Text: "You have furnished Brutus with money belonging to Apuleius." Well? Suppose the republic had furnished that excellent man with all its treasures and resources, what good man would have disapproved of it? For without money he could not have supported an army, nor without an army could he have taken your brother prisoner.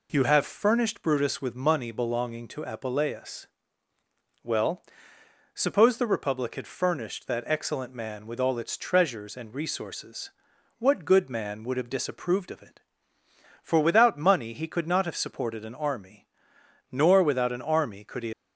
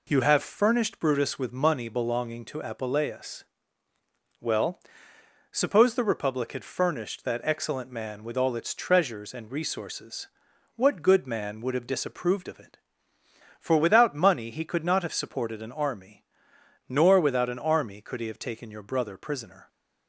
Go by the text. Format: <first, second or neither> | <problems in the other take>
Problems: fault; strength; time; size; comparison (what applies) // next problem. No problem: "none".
second | stops before "have taken your brother prisoner"; at 18.3 s